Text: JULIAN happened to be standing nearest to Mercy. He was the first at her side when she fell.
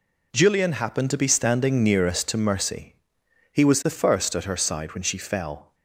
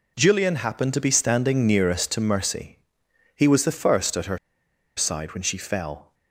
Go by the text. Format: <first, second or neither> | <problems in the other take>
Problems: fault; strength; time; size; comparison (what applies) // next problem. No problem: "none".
first | pauses between "her" and "side"; noticeable; at 4.3 s; 0.59 s long